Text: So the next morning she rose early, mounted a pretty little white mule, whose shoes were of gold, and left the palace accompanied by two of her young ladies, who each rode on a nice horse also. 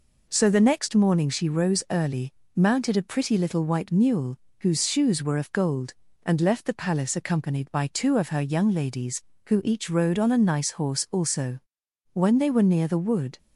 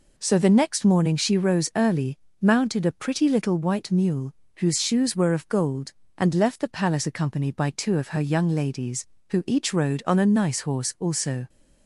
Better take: second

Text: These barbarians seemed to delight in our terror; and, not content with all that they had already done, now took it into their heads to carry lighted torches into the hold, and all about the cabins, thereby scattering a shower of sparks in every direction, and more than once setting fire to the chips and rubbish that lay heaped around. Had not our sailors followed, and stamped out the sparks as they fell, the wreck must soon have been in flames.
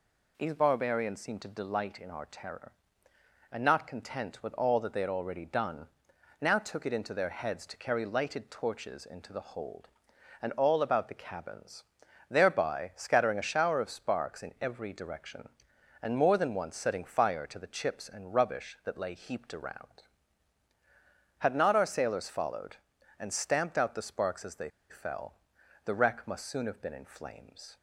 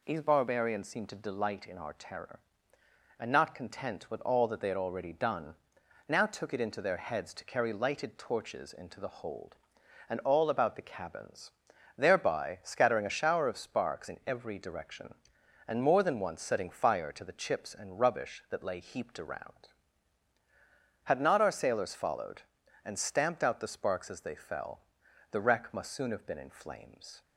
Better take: second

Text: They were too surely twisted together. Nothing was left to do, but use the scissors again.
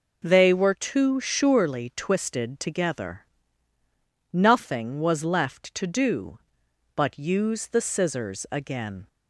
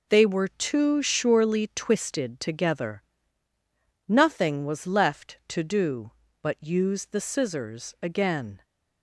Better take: neither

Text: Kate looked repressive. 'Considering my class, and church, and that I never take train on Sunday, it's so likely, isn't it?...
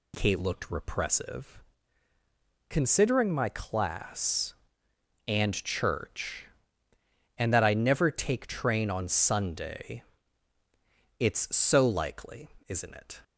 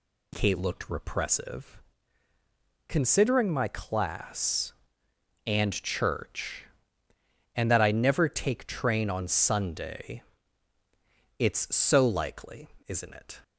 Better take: neither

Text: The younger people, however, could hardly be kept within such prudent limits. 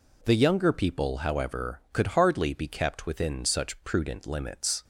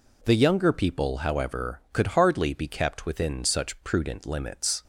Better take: neither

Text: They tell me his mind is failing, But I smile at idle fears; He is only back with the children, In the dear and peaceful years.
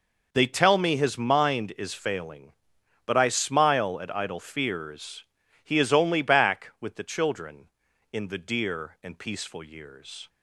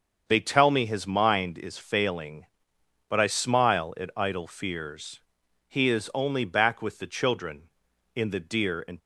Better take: first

